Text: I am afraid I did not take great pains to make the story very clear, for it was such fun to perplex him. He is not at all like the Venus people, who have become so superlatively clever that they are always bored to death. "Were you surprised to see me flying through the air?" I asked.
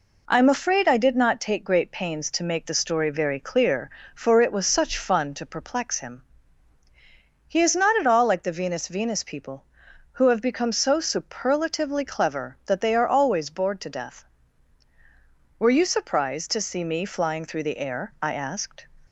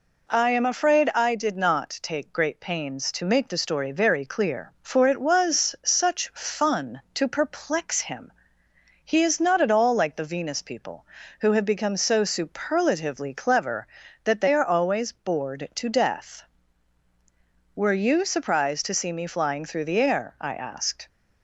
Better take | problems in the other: second | says "Venus" twice; at 8.8 s

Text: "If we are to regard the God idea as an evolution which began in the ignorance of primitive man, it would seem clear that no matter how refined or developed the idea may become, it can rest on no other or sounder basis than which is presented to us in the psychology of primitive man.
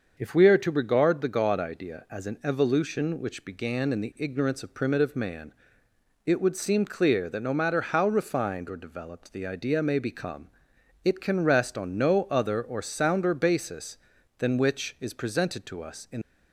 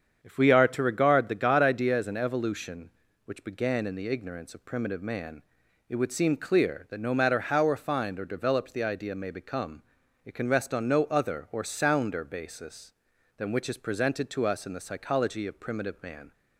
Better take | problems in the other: second | starts louder than the rest; until 1.1 s; 6.5 dB; strong in the second // stops before "the psychology of primitive man"; at 16.2 s

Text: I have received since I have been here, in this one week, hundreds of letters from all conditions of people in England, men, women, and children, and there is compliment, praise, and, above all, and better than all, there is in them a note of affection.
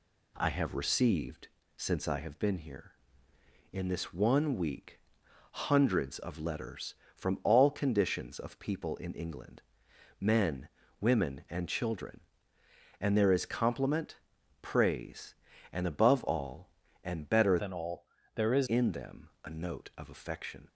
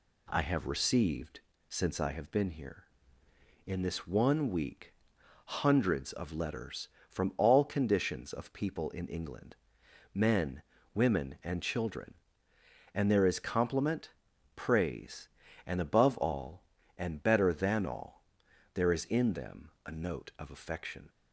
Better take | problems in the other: second | pauses between "received" and "since"; slight; at 1.4 s; 0.30 s long; slight in the second // changes voice from "than" to "is"; from 17.5 to 18.6 s; 1.1 s long // pauses between "them" and "a"; slight; at 19.2 s; 0.16 s long; slight in the second

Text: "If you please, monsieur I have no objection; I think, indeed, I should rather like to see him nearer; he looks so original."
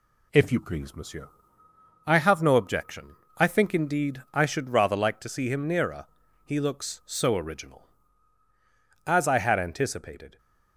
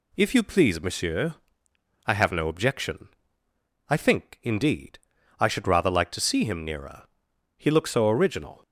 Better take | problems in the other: second | pauses between "monsieur" and "I"; noticeable; at 1.2 s; 0.78 s long; noticeable in the second // goes on to say "As I had anticipated"; from 9.0 s on; 1.3 s long

